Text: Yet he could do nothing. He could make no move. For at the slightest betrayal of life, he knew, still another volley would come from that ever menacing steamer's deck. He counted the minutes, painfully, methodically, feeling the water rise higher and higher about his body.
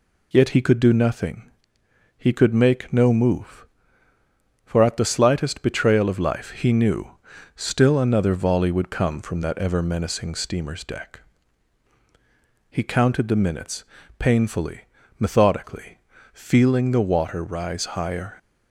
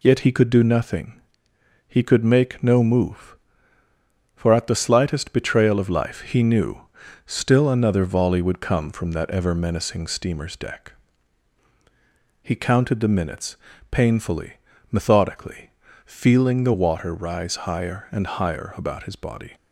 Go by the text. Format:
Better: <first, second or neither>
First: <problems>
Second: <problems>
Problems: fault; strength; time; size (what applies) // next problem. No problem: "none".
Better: second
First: stops before "and higher about his body"; at 18.3 s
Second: none